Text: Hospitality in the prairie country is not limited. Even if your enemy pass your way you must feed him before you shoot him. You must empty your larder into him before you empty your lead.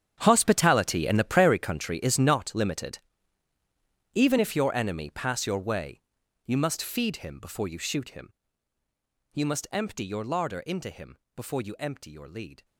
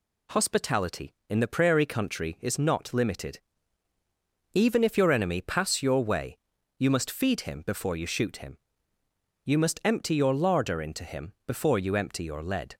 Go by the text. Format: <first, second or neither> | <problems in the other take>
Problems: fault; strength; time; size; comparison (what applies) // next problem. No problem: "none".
second | gets quieter; strong; throughout; 16.5 dB // pauses between "way" and "you"; noticeable; at 6.0 s; 0.46 s long; also in the second // pauses between "him" and "before"; slight; at 11.1 s; 0.18 s long